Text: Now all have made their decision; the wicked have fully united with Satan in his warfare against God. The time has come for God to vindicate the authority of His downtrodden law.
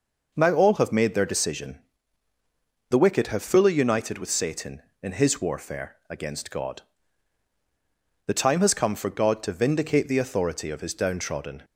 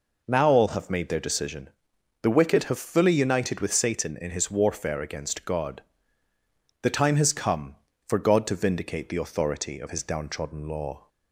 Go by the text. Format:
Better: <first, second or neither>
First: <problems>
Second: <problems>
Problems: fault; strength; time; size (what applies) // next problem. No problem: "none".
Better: second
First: stops before "law"; at 11.6 s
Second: none